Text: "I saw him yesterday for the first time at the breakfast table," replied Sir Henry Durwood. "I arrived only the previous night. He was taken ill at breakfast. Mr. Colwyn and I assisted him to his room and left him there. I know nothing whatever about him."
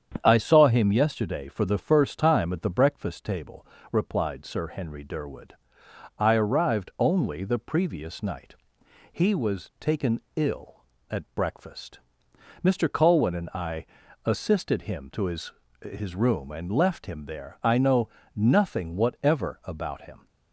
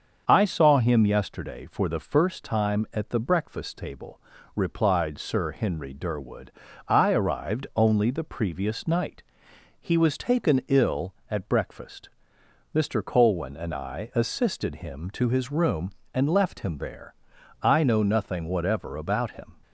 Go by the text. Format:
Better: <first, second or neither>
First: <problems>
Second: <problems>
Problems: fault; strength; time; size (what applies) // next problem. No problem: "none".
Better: second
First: starts louder than the rest; strong; until 1.2 s; 8.5 dB // pauses between "taken" and "ill"; slight; at 10.1 s; 0.16 s long // pauses between "I" and "assisted"; at 13.8 s; 0.40 s long // says "his" twice; at 15.7 s // pauses between "know" and "nothing"; slight; at 18.0 s; 0.26 s long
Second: starts louder than the rest; until 1.2 s; 7 dB